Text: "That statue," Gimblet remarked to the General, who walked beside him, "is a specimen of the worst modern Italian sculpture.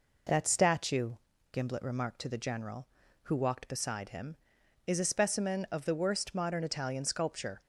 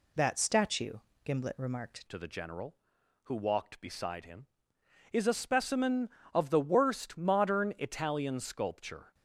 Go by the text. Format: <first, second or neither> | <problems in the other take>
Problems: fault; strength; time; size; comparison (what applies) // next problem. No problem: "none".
first | changes voice at "to"; from 2.0 s on; 7.1 s long